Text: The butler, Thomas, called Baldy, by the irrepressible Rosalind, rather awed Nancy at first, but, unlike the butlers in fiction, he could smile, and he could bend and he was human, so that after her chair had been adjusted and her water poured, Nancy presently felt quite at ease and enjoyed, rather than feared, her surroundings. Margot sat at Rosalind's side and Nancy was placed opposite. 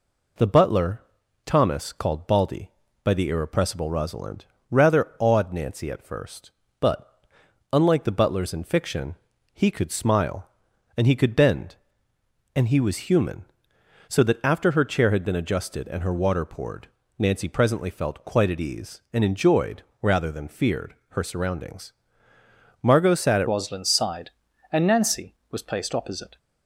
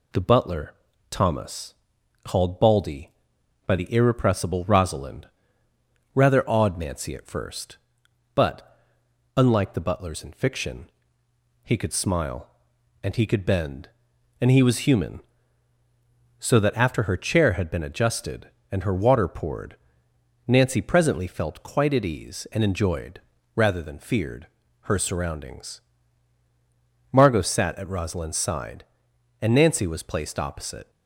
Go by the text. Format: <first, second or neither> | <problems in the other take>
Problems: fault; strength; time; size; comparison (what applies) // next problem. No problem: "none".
second | changes voice at "Rosalind's"; from 23.4 s on; 2.9 s long